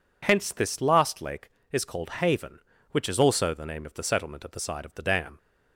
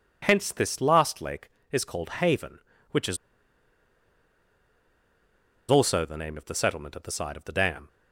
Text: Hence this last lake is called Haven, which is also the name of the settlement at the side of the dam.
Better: first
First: none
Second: pauses between "is" and "also"; strong; at 3.1 s; 2.5 s long

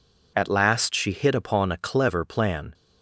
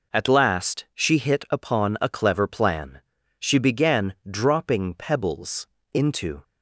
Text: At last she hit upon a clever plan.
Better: first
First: none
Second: goes on to say "She began dropping pebbles into"; strong; from 3.3 s on; 3.0 s long

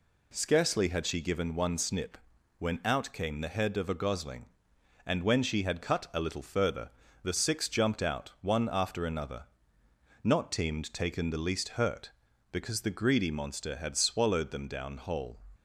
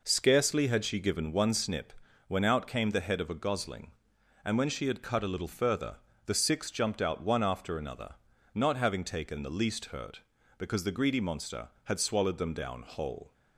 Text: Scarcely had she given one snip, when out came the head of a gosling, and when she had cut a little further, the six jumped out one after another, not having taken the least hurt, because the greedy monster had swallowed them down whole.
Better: second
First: says "teemed" for "having"; at 10.5 s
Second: none

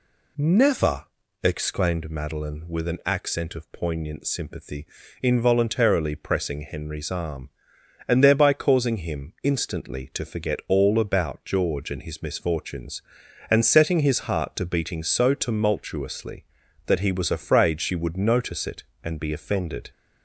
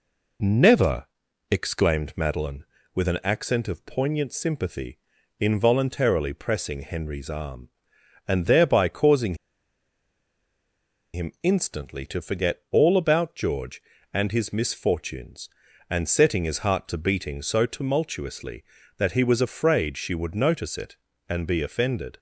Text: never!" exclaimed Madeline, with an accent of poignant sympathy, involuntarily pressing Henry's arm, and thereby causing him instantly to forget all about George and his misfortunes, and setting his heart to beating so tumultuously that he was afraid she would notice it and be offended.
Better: first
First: none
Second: pauses between "causing" and "him"; strong; at 9.3 s; 1.7 s long

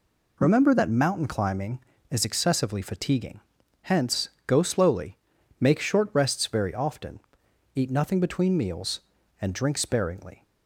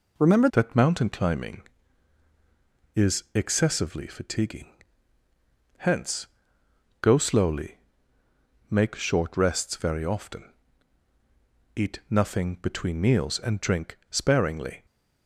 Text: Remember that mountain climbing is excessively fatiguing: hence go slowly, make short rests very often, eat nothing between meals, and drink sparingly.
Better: first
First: pauses between "hence" and "go"; slight; at 4.2 s; 0.16 s long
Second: changes voice at "that"; from 0.5 s on; 14.3 s long // pauses between "hence" and "go"; noticeable; at 6.2 s; 0.74 s long

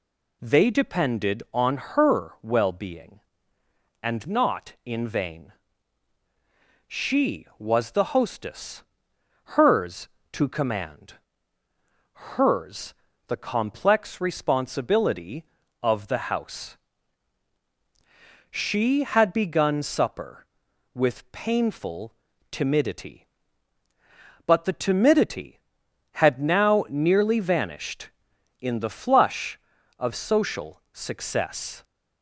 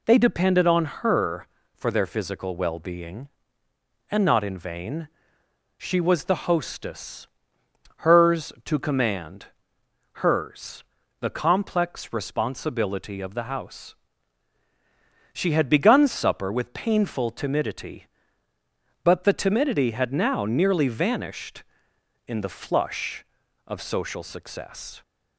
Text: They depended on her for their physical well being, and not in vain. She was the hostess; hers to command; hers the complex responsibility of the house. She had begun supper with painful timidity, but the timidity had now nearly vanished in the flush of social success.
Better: second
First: skips "for their physical"; at 2.3 s // pauses between "hers" and "the"; slight; at 12.9 s; 0.32 s long // pauses between "painful" and "timidity"; at 22.1 s; 0.38 s long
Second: pauses between "hers" and "the"; at 10.8 s; 0.38 s long

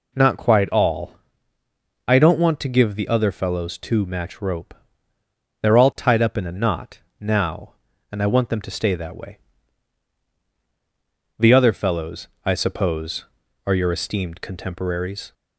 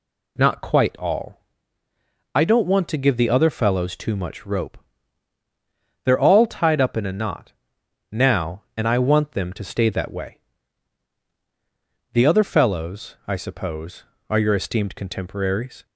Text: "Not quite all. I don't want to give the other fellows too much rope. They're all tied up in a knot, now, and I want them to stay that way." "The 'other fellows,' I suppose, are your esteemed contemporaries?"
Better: second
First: says "match" for "much"; at 4.0 s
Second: none

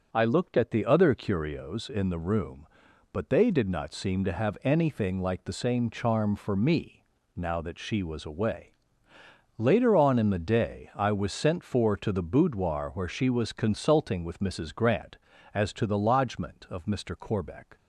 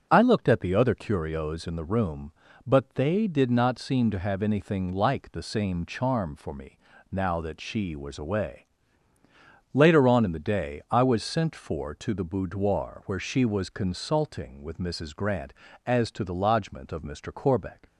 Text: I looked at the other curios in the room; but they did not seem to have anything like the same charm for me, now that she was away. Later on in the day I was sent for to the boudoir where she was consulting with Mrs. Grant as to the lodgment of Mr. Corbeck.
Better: neither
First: starts louder than the rest; until 1.1 s; 6.5 dB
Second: starts louder than the rest; until 1.1 s; 7 dB

